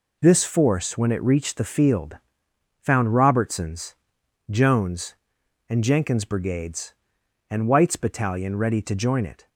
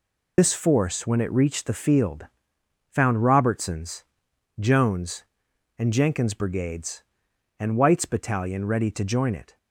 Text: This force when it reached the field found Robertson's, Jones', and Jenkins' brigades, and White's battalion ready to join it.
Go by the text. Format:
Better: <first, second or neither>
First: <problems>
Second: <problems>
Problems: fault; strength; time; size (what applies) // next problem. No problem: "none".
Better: first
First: pauses between "field" and "found"; noticeable; at 2.1 s; 0.62 s long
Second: loses the start of "This"; at 0.3 s; 90 ms // pauses between "field" and "found"; noticeable; at 2.2 s; 0.62 s long